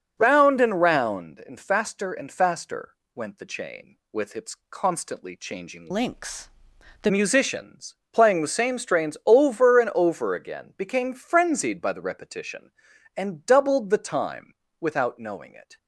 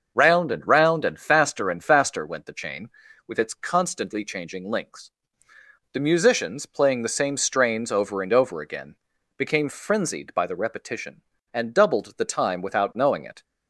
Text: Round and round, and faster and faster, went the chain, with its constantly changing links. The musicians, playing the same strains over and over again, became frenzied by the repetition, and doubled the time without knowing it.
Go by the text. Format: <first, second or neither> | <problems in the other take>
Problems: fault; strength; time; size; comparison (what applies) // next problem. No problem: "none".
second | starts louder than the rest; until 1.2 s; 6 dB; also in the second // pauses between "its" and "constantly"; slight; at 4.5 s; 0.16 s long // changes voice from "links" to "The"; from 5.9 to 7.1 s; 1.2 s long // pauses between "time" and "without"; slight; at 14.5 s; 0.26 s long